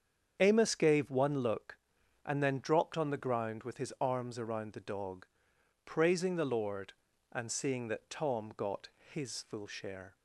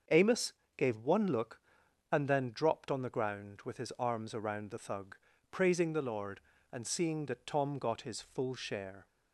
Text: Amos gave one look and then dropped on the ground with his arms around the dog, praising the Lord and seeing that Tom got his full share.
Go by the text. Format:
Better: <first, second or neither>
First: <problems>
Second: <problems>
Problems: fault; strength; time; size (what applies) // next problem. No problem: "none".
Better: first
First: starts louder than the rest; strong; until 1.4 s; 7.5 dB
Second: starts louder than the rest; until 1.3 s; 6.5 dB // pauses between "Amos" and "gave"; slight; at 0.5 s; 0.24 s long // says "thug" for "dog"; at 4.7 s